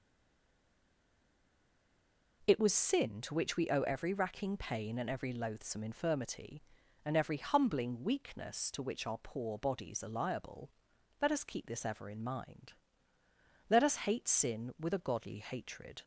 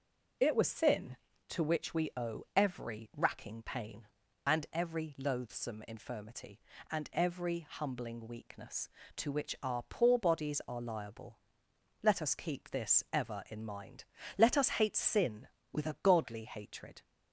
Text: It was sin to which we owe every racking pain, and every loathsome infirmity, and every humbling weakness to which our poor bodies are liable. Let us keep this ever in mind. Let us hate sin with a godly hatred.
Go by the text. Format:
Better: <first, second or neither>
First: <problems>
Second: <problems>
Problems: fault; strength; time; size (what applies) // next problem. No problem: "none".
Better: second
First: stays silent before the first word; until 2.4 s; 2.4 s long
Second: none